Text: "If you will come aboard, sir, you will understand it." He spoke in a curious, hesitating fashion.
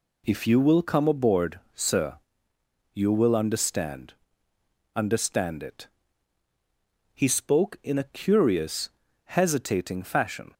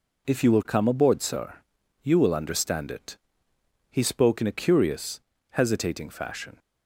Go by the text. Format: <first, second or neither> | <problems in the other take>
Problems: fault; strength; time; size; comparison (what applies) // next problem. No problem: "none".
second | says "understand" twice; at 4.9 s